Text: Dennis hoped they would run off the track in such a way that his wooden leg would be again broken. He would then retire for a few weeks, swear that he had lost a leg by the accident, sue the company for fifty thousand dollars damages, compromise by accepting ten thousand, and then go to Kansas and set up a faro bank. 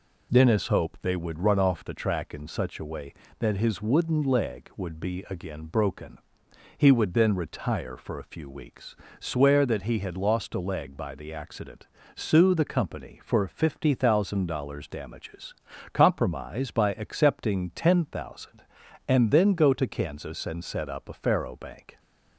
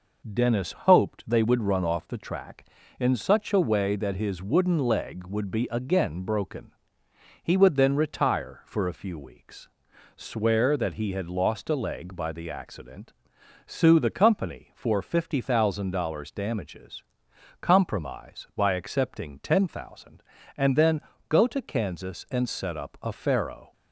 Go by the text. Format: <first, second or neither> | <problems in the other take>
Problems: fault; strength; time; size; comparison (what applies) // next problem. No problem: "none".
first | pauses between "then" and "go"; slight; at 21.0 s; 0.28 s long // stops before "bank"; at 23.7 s